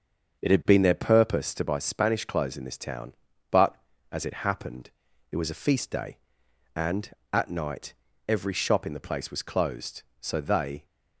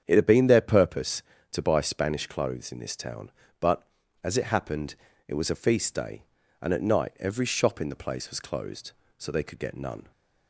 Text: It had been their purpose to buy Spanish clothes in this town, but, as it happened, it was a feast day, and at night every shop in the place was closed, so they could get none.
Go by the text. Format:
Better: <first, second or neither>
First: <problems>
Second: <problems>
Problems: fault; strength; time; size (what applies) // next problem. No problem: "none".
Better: second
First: starts louder than the rest; until 1.4 s; 6.5 dB // pauses between "night" and "every"; slight; at 7.9 s; 0.34 s long // stops before "could get none"; at 10.8 s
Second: starts louder than the rest; strong; until 1.0 s; 8 dB